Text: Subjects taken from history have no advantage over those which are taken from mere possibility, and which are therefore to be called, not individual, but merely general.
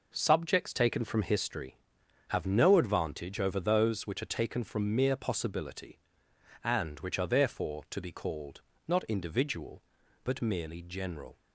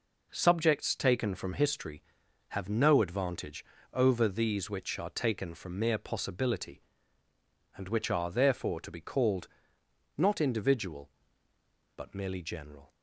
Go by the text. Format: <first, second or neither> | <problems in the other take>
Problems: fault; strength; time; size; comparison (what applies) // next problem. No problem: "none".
first | pauses between "advantage" and "over"; slight; at 3.6 s; 0.30 s long // says "these" for "those"; at 4.2 s